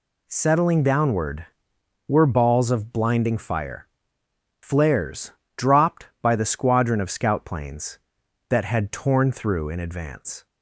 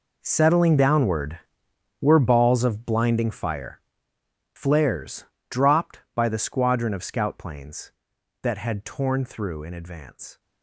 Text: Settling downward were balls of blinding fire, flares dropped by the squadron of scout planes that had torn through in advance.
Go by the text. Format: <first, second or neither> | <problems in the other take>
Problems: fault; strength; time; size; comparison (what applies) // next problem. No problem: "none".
first | gets quieter; strong; throughout; 16.5 dB // pauses between "flares" and "dropped"; slight; at 5.2 s; 0.24 s long; slight in the first